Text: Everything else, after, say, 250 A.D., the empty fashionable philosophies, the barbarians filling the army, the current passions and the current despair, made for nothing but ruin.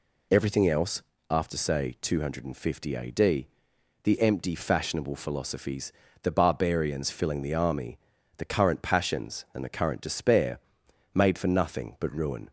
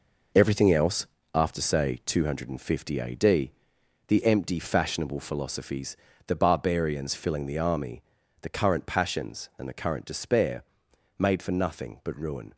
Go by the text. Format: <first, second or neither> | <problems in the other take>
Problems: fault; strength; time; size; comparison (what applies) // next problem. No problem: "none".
first | gets quieter; strong; throughout; 9 dB